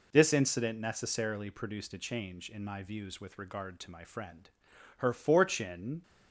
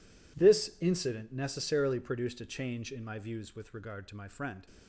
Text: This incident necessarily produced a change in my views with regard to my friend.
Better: second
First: goes on to say "Her fortune"; noticeable; from 4.9 s on; 1.0 s long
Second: none

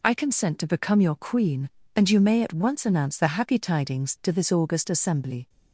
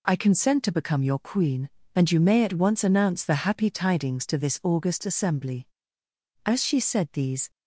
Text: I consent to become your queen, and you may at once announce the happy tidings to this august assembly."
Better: first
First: none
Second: goes on to say "As she said these"; noticeable; from 6.4 s on; 1.0 s long

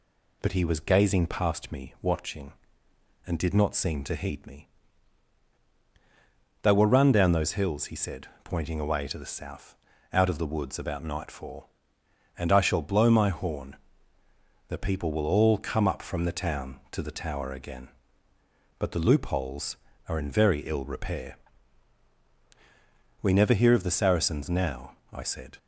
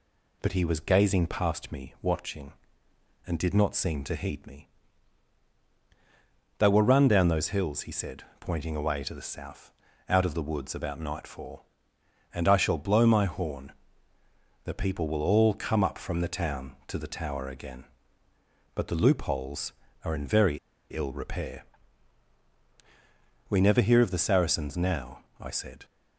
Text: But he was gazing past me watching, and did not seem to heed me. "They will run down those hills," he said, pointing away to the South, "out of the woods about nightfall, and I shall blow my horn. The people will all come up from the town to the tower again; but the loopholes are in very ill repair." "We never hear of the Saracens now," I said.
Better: first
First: none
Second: pauses between "very" and "ill"; slight; at 20.5 s; 0.33 s long

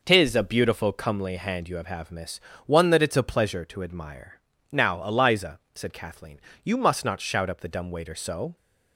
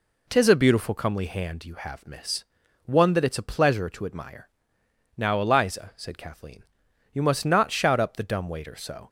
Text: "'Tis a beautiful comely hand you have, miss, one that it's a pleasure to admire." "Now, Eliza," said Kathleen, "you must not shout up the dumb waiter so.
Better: second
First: says "have" twice; at 1.8 s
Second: none

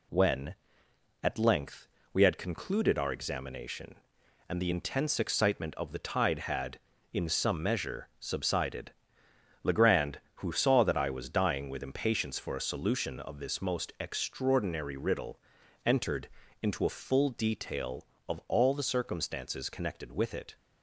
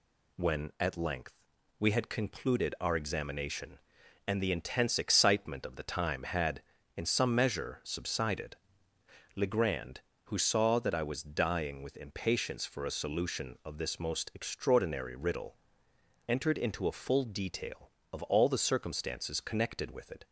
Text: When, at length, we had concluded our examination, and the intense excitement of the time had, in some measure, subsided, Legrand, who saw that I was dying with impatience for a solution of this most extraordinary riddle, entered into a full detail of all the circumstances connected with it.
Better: second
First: says "tide" for "time"; at 5.9 s // pauses between "entered" and "into"; slight; at 16.2 s; 0.34 s long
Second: none

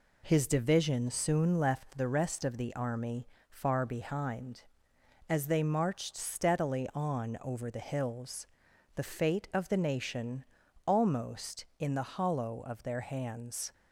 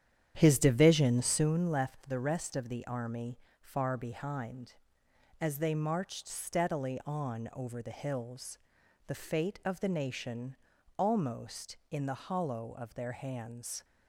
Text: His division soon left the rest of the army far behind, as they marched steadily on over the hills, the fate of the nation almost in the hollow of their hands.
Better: first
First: pauses between "army" and "far"; slight; at 3.2 s; 0.22 s long // pauses between "nation" and "almost"; at 10.4 s; 0.42 s long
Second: starts louder than the rest; strong; until 1.5 s; 9.5 dB // pauses between "army" and "far"; slight; at 3.3 s; 0.22 s long // pauses between "nation" and "almost"; at 10.5 s; 0.42 s long

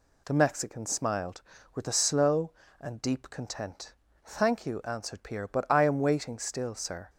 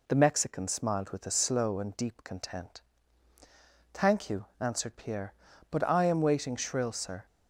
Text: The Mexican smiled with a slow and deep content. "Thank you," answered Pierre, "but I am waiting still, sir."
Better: first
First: none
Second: says "shrill" for "still"; at 6.5 s

